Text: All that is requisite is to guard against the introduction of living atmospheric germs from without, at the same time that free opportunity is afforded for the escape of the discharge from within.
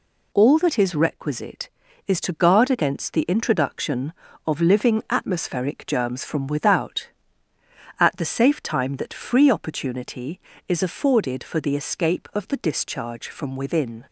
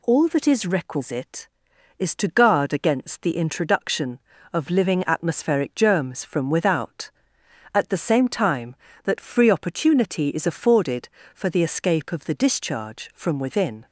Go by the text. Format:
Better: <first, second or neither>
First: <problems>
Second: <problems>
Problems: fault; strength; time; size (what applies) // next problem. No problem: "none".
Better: second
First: says "safe" for "same"; at 8.2 s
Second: none